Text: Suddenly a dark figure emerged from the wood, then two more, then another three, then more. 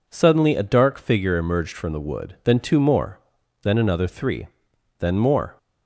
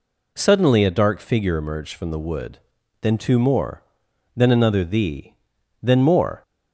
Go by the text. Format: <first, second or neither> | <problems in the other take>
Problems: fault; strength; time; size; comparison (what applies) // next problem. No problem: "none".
first | says "thee" for "three"; at 4.8 s